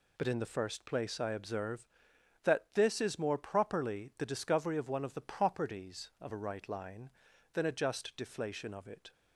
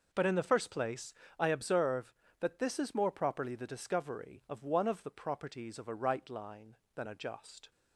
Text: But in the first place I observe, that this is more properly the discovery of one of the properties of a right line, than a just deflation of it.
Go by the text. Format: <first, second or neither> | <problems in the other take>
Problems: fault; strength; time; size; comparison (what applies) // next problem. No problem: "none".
first | pauses between "place" and "I"; slight; at 1.1 s; 0.26 s long // stops before "deflation of it"; at 7.7 s